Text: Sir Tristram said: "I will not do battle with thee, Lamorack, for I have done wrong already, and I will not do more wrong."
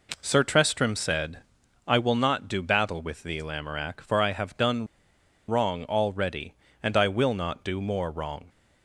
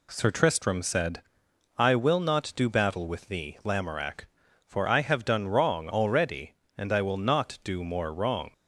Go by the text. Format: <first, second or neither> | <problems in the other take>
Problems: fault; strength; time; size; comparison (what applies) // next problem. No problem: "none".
second | pauses between "done" and "wrong"; noticeable; at 4.8 s; 0.63 s long